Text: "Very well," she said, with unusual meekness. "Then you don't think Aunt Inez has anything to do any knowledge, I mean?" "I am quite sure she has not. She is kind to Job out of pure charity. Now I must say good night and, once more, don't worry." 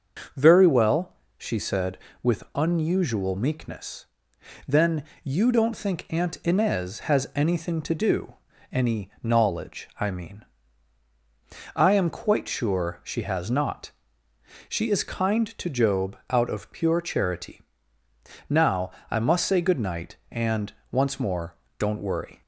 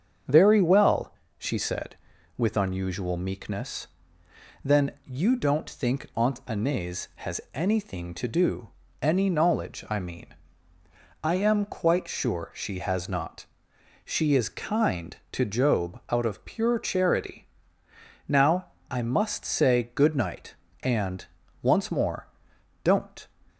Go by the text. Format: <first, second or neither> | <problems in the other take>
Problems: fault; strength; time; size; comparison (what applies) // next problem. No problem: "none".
first | starts louder than the rest; until 1.5 s; 6.5 dB; also in the first // pauses between "Then" and "you"; slight; at 4.8 s; 0.16 s long; slight in the first // pauses between "do" and "any"; slight; at 8.6 s; 0.30 s long; also in the first // pauses between "Now" and "I"; slight; at 18.7 s; 0.18 s long; slight in the first // stops before "worry"; at 23.4 s